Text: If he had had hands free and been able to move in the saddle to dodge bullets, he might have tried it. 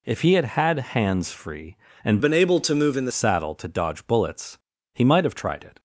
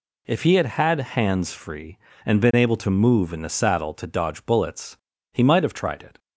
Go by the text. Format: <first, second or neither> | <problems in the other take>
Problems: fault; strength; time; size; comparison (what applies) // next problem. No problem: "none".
second | changes voice from "been" to "the"; from 2.2 to 3.1 s; 0.9 s long